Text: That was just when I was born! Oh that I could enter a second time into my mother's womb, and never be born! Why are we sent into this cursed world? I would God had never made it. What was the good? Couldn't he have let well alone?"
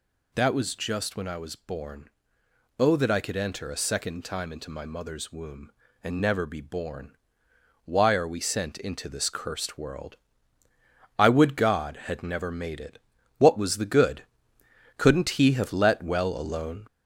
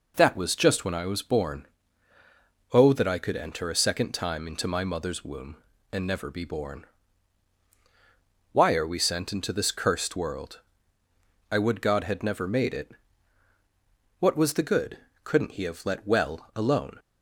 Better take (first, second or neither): second